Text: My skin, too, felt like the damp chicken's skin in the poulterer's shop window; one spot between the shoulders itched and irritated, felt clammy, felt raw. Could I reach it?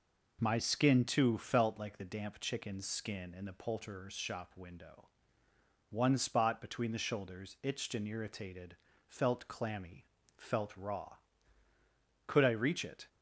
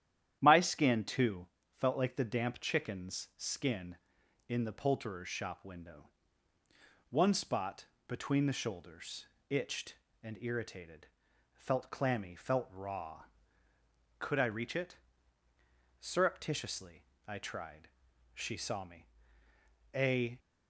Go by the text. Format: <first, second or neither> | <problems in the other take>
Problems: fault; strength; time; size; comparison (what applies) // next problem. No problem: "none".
first | starts louder than the rest; strong; until 1.4 s; 10.5 dB // pauses between "spot" and "between"; slight; at 7.8 s; 0.20 s long // pauses between "shoulders" and "itched"; slight; at 9.2 s; 0.24 s long // goes on to say "Surreptitiously I tried She saw me A"; strong; from 16.0 s on; 4.3 s long